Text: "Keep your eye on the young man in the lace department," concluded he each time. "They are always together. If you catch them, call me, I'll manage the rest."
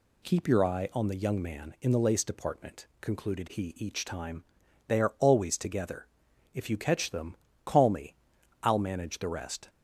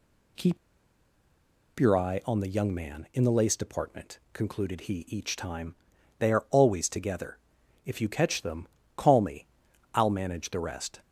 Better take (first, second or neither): first